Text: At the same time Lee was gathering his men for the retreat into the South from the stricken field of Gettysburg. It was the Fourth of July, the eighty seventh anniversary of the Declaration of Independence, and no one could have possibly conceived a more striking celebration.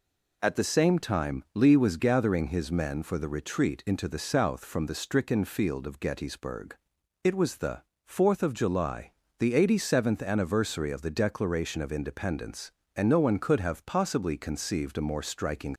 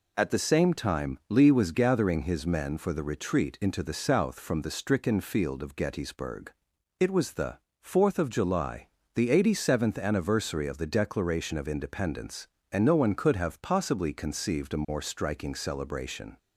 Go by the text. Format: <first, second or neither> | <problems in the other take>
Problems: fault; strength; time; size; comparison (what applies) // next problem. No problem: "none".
second | pauses between "the" and "Fourth"; slight; at 7.8 s; 0.22 s long; slight in the second // stops before "celebration"; at 15.7 s